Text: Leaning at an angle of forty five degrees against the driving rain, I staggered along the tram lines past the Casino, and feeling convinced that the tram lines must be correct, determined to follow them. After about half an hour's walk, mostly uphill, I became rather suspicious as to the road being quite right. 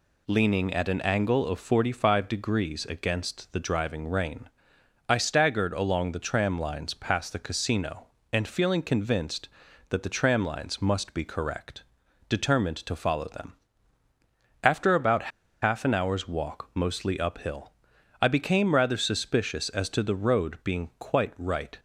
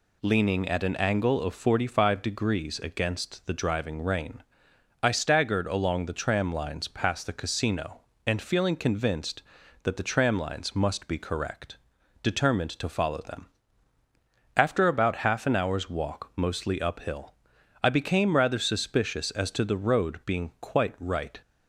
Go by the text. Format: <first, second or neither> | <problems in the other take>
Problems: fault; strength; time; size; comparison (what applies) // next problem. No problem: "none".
second | pauses between "about" and "half"; slight; at 15.3 s; 0.33 s long